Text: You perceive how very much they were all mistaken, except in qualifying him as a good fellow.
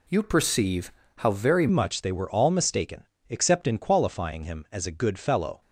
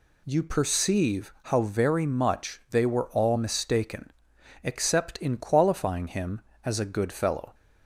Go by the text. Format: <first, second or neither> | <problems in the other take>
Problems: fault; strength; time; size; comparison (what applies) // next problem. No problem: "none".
second | pauses between "perceive" and "how"; slight; at 0.9 s; 0.26 s long // changes voice at "much"; from 1.6 s on; 4.0 s long